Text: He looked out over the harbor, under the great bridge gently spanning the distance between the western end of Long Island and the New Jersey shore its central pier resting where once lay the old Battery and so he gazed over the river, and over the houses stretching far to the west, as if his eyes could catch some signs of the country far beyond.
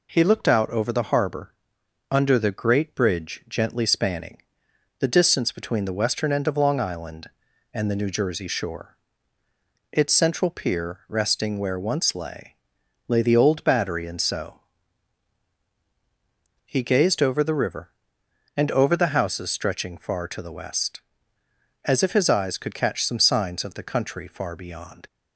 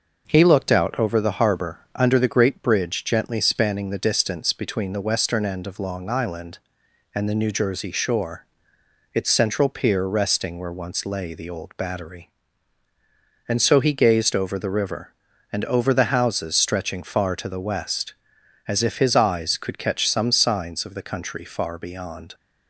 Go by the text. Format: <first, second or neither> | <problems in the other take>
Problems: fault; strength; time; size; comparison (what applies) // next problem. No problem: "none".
second | pauses between "spanning" and "the"; noticeable; at 4.4 s; 0.56 s long // pauses between "shore" and "its"; noticeable; at 8.9 s; 0.96 s long; noticeable in the second // says "lay" twice; at 13.0 s // pauses between "so" and "he"; strong; at 14.5 s; 2.0 s long